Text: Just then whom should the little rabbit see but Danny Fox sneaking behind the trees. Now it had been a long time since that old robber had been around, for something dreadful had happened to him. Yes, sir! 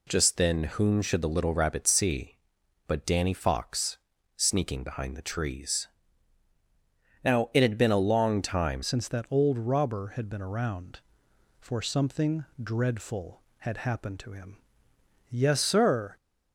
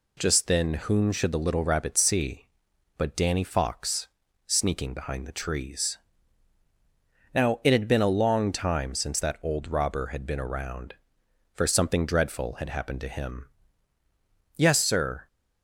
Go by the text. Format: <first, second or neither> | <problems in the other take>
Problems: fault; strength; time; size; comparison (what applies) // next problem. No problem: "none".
second | pauses between "Fox" and "sneaking"; at 3.9 s; 0.40 s long; also in the second // changes voice at "since"; from 8.8 s on; 7.3 s long // pauses between "something" and "dreadful"; slight; at 12.4 s; 0.18 s long